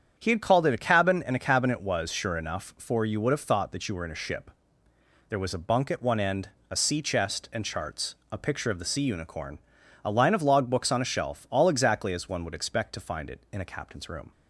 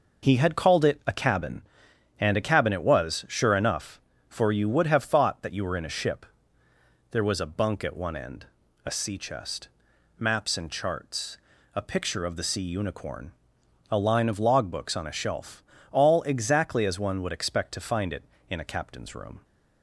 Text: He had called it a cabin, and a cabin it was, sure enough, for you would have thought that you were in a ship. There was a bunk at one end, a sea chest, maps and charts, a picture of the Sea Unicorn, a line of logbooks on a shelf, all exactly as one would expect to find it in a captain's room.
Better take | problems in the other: second | starts louder than the rest; strong; until 1.1 s; 8 dB // skips "maps"; at 7.5 s

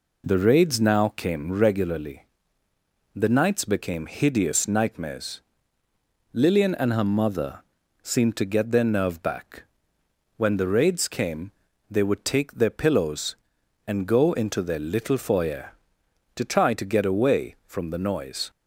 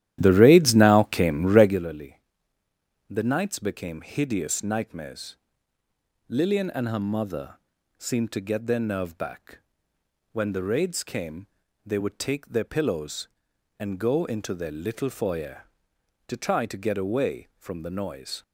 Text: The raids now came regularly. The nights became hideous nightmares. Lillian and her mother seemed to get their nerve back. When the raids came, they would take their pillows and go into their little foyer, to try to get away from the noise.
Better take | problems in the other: first | starts louder than the rest; strong; until 1.8 s; 12.5 dB // pauses between "mother" and "seemed"; at 7.5 s; 0.44 s long; also in the first

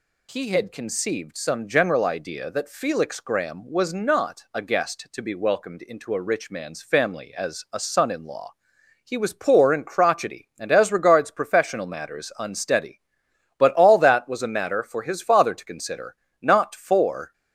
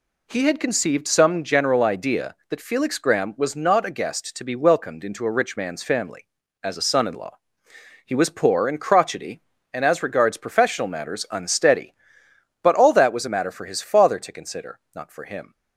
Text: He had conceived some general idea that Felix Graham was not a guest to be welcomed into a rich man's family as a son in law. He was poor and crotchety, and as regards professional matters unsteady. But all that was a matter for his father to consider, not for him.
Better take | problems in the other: second | stops before "him"; at 17.3 s

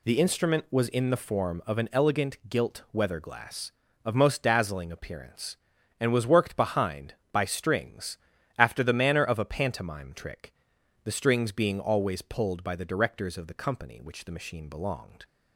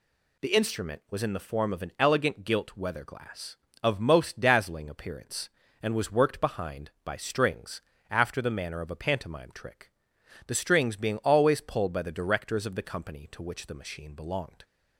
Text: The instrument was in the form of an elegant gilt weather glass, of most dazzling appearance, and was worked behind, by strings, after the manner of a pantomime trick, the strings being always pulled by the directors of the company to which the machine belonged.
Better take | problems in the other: second | skips "to"; at 14.0 s

